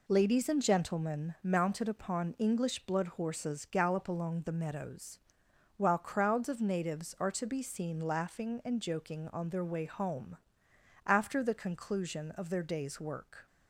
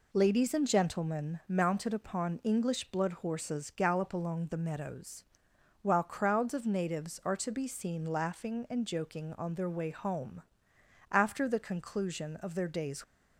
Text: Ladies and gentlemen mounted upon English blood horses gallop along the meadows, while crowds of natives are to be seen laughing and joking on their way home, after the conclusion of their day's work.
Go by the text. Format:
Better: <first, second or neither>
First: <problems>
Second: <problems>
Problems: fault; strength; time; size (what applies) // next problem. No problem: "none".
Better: first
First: none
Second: stops before "work"; at 13.0 s